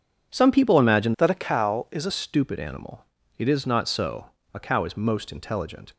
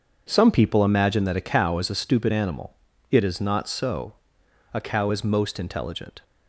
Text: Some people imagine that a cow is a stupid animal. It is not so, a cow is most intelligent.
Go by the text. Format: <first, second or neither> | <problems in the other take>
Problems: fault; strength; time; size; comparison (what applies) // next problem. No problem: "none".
second | starts louder than the rest; strong; until 1.3 s; 7.5 dB // changes voice from "that" to "a"; from 1.1 to 2.1 s; 1.0 s long